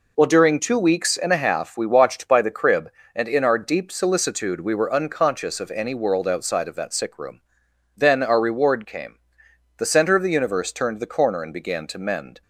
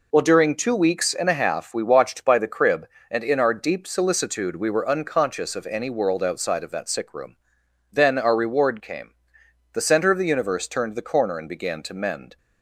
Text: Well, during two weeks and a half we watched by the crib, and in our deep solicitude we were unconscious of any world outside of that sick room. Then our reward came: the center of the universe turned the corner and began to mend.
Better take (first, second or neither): neither